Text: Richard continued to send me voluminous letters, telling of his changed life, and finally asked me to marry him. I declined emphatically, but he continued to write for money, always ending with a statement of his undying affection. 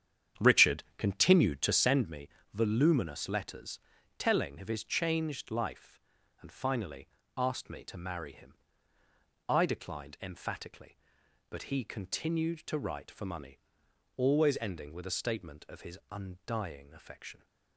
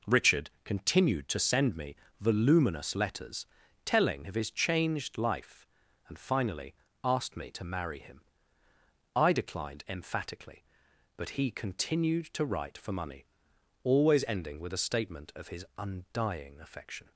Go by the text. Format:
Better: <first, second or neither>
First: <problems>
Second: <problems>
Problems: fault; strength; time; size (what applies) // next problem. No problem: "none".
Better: second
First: starts louder than the rest; strong; until 2.1 s; 9 dB // pauses between "Richard" and "continued"; slight; at 0.8 s; 0.16 s long // pauses between "me" and "voluminous"; slight; at 2.2 s; 0.24 s long // pauses between "finally" and "asked"; slight; at 7.0 s; 0.30 s long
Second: pauses between "Richard" and "continued"; slight; at 0.4 s; 0.16 s long // pauses between "me" and "voluminous"; slight; at 1.9 s; 0.24 s long // pauses between "finally" and "asked"; slight; at 6.7 s; 0.30 s long